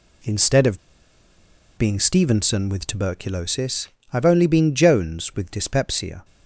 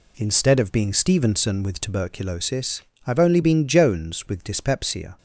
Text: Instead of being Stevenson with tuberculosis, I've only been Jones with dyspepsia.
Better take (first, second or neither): second